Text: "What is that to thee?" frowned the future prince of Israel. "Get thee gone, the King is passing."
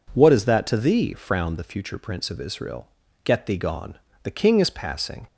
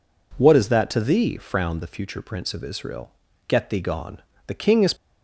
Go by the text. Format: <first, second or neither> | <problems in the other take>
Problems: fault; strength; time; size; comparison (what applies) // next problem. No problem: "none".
first | stops before "passing"; at 4.9 s